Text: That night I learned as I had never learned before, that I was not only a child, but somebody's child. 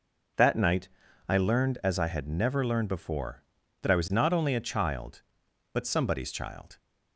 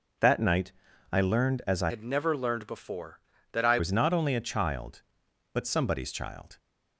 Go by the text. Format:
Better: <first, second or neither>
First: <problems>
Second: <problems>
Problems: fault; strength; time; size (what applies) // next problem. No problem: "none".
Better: first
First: pauses between "night" and "I"; at 0.8 s; 0.40 s long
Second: pauses between "night" and "I"; at 0.7 s; 0.40 s long // changes voice from "had" to "I"; from 1.8 to 3.7 s; 1.9 s long